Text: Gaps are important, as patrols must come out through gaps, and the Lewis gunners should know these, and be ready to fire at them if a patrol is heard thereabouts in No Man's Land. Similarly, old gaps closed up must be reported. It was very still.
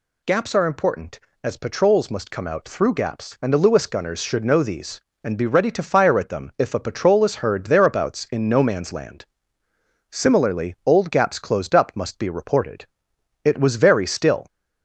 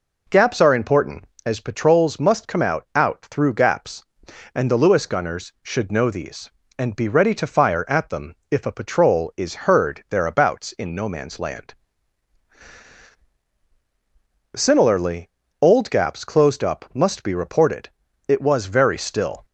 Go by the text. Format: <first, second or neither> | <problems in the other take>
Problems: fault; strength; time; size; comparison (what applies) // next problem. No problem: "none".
first | says "out" twice; at 2.9 s // pauses between "them" and "if"; slight; at 8.3 s; 0.16 s long